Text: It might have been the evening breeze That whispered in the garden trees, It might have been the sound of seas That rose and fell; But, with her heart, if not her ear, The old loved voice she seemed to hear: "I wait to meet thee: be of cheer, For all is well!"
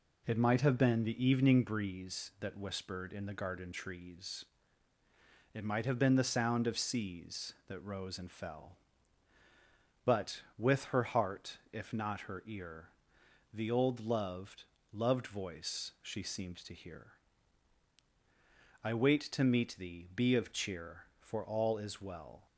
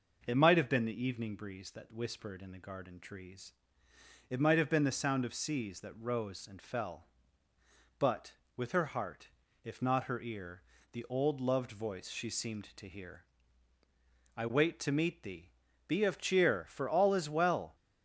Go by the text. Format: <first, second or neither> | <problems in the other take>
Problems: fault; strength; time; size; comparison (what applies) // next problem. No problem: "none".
second | says "loved" twice; at 14.9 s